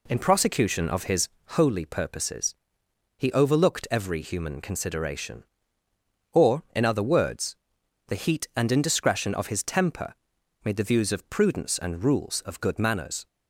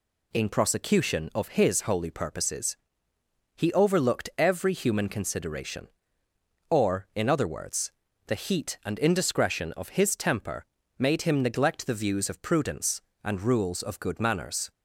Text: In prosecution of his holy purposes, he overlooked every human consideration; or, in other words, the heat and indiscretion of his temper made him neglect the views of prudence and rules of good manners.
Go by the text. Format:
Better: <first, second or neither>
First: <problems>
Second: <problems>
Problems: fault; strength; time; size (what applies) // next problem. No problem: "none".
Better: second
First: pauses between "his" and "holy"; slight; at 1.2 s; 0.20 s long // pauses between "temper" and "made"; noticeable; at 10.1 s; 0.48 s long // skips "him neglect"; at 10.7 s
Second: pauses between "temper" and "made"; slight; at 10.6 s; 0.34 s long